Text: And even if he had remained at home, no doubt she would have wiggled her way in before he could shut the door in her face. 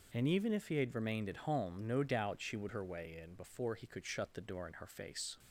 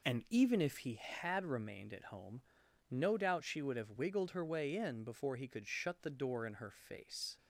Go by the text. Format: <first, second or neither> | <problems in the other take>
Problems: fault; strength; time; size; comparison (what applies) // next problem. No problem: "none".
second | skips "have wiggled"; at 2.6 s